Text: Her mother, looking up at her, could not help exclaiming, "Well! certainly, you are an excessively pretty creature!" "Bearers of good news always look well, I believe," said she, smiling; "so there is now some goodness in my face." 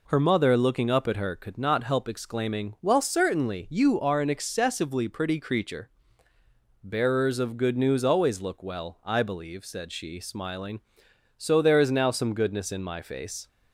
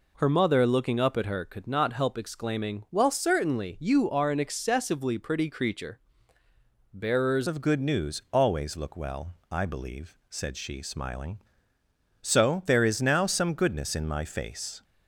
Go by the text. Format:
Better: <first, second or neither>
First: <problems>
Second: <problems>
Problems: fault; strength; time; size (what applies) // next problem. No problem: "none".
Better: first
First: none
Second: changes voice at "of"; from 7.4 s on; 7.4 s long